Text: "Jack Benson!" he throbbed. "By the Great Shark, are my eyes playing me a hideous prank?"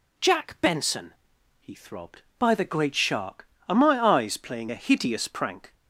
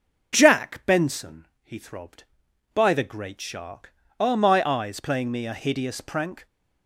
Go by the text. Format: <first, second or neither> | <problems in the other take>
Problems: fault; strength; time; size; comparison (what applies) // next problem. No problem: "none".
second | skips "me"; at 4.7 s